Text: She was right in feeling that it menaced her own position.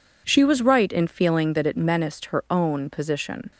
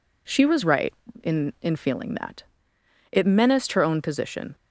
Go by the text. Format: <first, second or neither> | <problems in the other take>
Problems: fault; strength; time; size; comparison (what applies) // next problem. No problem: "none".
first | says "in" twice; at 1.6 s // pauses between "that" and "it"; noticeable; at 2.4 s; 0.66 s long